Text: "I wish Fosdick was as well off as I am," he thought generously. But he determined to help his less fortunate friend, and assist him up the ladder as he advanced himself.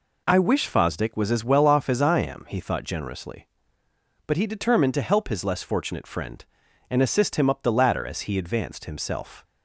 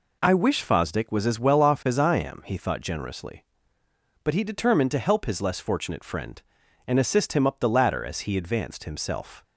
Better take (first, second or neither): neither